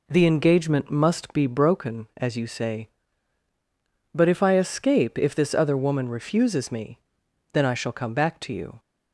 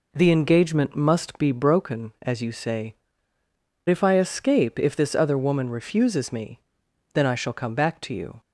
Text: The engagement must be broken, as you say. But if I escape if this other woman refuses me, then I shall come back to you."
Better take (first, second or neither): first